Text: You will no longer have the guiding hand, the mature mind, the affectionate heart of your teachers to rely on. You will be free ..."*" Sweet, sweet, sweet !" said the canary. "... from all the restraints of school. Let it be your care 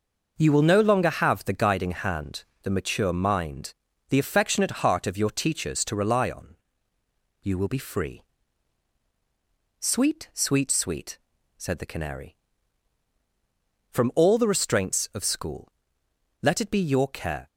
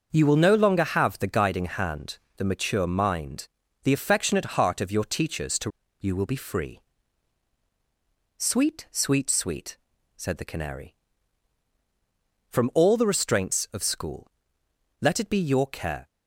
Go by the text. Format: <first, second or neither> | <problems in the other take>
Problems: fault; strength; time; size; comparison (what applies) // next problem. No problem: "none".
first | starts louder than the rest; until 1.1 s; 6.5 dB; also in the first // skips "rely on"; at 5.8 s